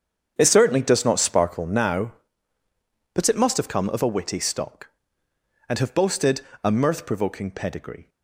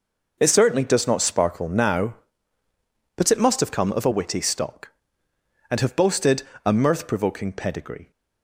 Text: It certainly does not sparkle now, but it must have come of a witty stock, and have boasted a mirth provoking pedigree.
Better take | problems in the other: second | starts louder than the rest; strong; until 1.8 s; 7.5 dB // pauses between "boasted" and "a"; slight; at 6.4 s; 0.22 s long; slight in the second

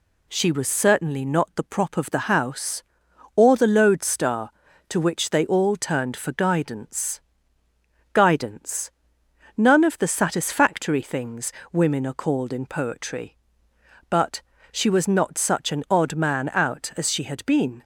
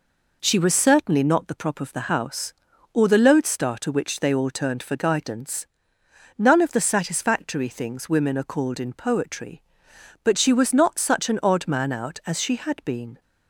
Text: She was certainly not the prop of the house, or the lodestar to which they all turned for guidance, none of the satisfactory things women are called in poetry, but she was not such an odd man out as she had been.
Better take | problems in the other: second | says "guidance" twice; at 8.1 s // pauses between "things" and "women"; slight; at 11.5 s; 0.18 s long // pauses between "but" and "she"; slight; at 14.4 s; 0.30 s long

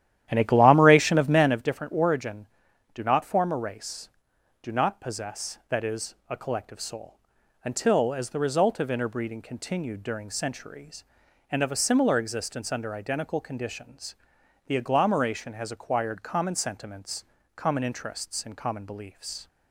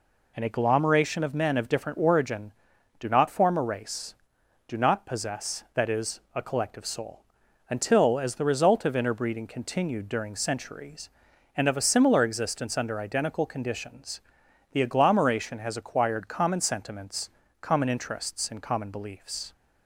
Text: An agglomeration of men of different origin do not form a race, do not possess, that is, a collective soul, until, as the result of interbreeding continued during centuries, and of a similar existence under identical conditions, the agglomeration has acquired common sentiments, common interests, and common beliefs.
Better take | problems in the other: second | starts louder than the rest; strong; until 1.6 s; 11.5 dB

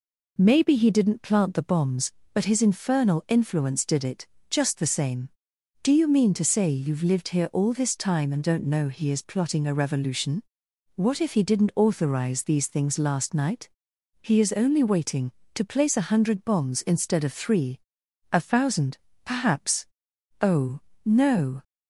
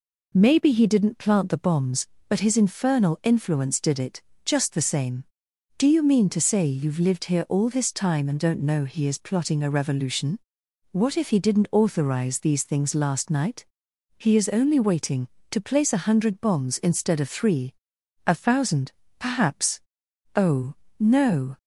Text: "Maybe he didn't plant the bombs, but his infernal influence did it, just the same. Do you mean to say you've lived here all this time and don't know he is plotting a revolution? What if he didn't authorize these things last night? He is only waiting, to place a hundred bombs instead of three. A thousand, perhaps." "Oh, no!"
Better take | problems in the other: neither | none

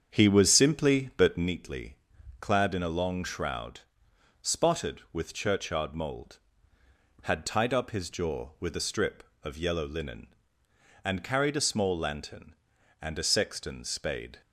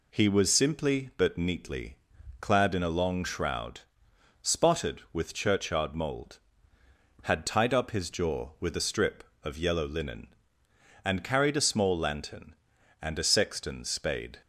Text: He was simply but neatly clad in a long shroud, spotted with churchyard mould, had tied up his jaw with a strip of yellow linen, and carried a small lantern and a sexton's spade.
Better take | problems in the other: second | starts louder than the rest; strong; until 1.6 s; 7.5 dB // pauses between "neatly" and "clad"; noticeable; at 1.9 s; 0.46 s long; noticeable in the second

